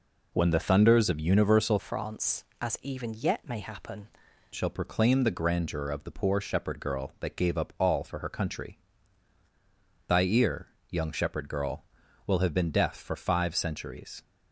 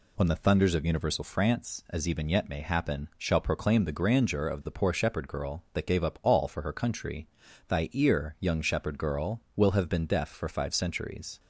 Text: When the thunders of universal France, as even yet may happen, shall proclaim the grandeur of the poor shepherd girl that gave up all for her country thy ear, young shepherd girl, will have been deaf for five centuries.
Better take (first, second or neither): second